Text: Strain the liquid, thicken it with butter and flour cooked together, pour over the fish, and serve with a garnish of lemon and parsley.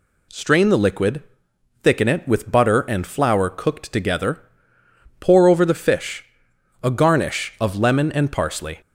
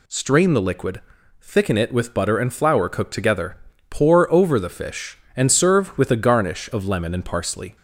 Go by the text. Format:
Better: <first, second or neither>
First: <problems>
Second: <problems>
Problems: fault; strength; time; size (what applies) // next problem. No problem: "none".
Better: second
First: skips "and serve with"; at 6.5 s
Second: none